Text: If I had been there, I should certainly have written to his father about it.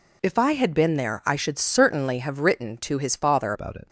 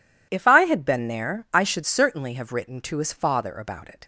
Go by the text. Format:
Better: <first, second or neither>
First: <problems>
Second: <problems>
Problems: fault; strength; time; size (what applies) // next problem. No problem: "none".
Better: second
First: changes voice at "about"; from 3.5 s on; 0.3 s long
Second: none